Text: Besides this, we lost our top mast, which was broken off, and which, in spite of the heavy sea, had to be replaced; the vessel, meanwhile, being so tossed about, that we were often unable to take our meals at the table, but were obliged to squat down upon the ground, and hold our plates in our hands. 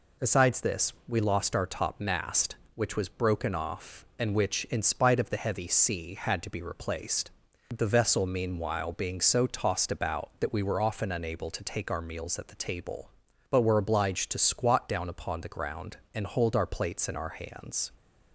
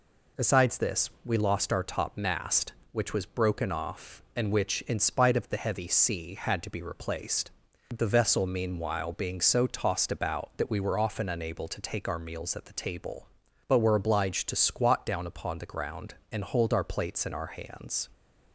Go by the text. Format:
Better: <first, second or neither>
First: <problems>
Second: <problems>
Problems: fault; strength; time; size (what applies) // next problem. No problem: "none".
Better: neither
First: none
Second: none